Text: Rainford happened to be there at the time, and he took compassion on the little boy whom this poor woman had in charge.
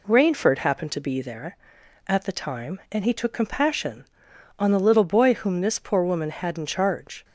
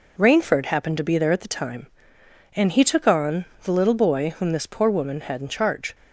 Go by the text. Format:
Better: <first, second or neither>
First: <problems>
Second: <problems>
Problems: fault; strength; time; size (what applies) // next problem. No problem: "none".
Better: first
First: none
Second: skips "compassion"; at 3.0 s // pauses between "on" and "the"; slight; at 3.4 s; 0.18 s long